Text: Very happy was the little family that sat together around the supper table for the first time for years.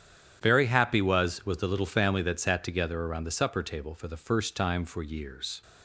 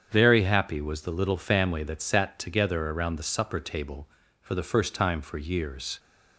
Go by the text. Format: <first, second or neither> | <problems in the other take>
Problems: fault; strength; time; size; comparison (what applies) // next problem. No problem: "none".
second | starts louder than the rest; strong; until 1.4 s; 9 dB; strong in the second // says "was" twice; at 1.4 s